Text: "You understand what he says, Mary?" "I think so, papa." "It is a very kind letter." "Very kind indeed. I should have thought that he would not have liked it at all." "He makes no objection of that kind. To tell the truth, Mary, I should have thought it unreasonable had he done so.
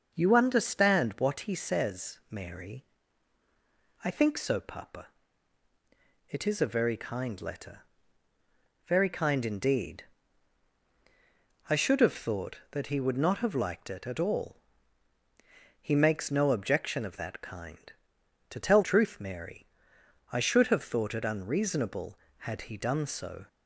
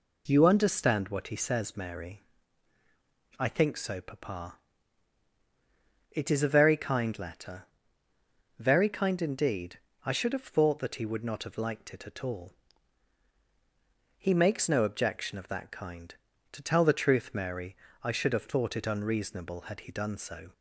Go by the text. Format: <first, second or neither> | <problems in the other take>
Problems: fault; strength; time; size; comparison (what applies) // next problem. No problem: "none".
second | starts louder than the rest; noticeable; until 1.1 s; 6 dB // skips "the"; at 18.8 s